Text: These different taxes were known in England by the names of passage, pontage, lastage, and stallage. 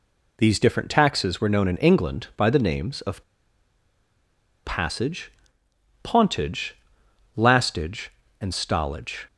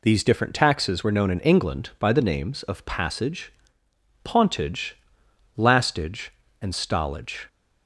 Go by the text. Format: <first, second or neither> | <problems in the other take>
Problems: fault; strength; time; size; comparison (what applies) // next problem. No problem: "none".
second | pauses between "of" and "passage"; strong; at 3.2 s; 1.4 s long